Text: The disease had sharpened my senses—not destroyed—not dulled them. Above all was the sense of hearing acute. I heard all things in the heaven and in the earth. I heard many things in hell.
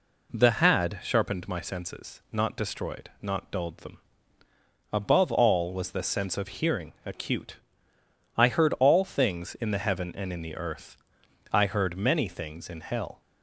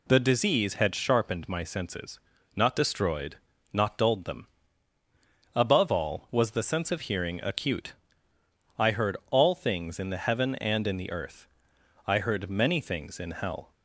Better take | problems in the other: second | skips "disease"; at 0.5 s

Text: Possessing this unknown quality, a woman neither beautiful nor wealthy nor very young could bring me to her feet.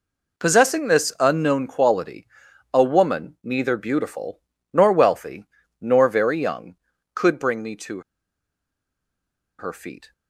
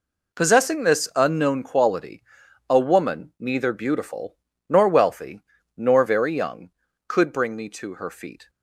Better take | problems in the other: second | pauses between "beautiful" and "nor"; slight; at 4.4 s; 0.32 s long; slight in the second // pauses between "wealthy" and "nor"; slight; at 5.4 s; 0.34 s long; slight in the second // pauses between "to" and "her"; strong; at 8.0 s; 1.5 s long

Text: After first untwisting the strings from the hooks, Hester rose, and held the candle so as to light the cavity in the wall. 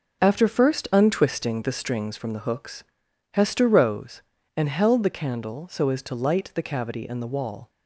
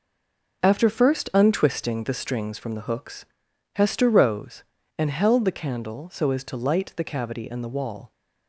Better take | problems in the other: first | stays silent before the first word; slight; until 0.6 s; 0.6 s long

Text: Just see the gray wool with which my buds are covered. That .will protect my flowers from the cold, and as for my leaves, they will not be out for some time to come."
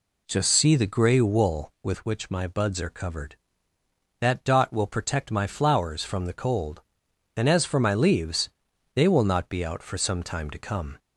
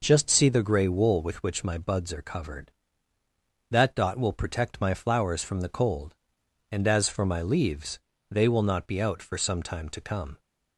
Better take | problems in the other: neither | none

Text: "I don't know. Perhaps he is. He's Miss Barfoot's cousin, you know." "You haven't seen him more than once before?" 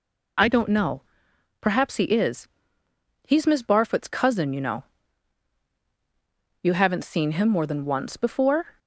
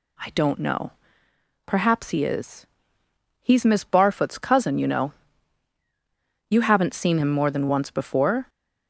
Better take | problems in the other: neither | none

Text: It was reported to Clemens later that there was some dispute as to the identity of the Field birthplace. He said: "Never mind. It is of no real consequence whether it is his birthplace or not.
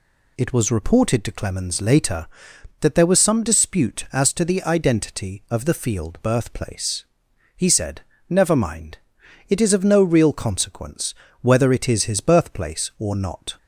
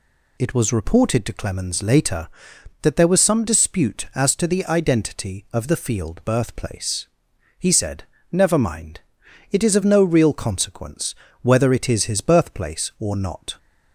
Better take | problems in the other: neither | pauses between "consequence" and "whether"; slight; the same in both

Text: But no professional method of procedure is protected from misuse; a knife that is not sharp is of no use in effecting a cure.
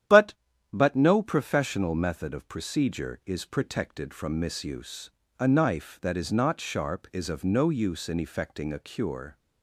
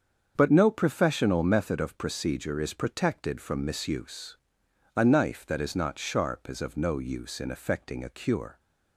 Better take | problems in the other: second | starts louder than the rest; strong; until 1.5 s; 10.5 dB; strong in the second // says "But" twice; at 0.7 s

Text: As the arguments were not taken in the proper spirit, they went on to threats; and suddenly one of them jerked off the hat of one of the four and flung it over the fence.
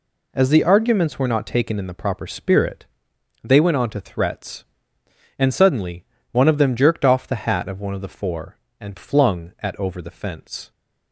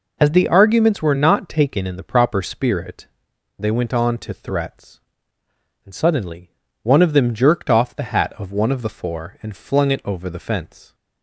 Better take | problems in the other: second | pauses between "suddenly" and "one"; slight; at 6.0 s; 0.26 s long; slight in the second // says "at" for "it"; at 9.6 s

